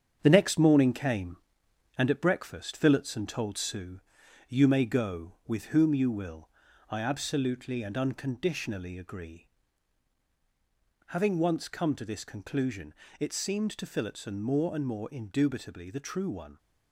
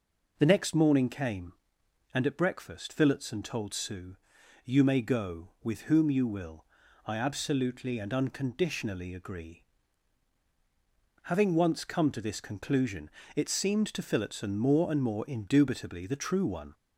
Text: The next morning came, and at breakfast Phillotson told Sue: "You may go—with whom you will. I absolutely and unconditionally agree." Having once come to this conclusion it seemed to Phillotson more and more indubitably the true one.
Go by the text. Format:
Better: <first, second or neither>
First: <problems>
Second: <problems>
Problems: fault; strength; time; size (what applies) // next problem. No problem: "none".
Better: second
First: gets quieter; throughout; 6 dB // pauses between "conclusion" and "it"; slight; at 12.9 s; 0.24 s long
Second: pauses between "conclusion" and "it"; slight; at 13.0 s; 0.24 s long